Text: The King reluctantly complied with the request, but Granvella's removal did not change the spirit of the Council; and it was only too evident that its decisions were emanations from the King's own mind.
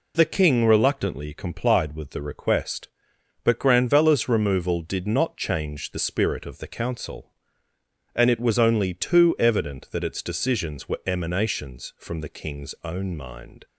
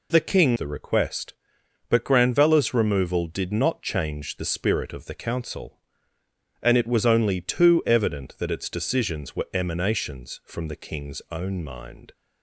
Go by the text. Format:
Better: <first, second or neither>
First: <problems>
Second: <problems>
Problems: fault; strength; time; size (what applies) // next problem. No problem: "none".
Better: first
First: none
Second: skips "reluctantly complied with"; at 0.5 s